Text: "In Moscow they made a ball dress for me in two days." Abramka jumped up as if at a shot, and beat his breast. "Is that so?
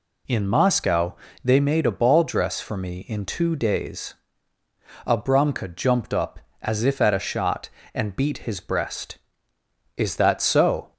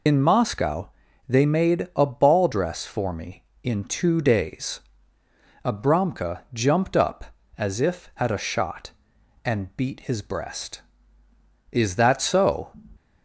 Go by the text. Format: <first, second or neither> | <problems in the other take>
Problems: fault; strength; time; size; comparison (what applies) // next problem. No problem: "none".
first | loses the start of "In"; at 0.0 s; 60 ms // pauses between "Moscow" and "they"; slight; at 0.8 s; 0.36 s long; slight in the first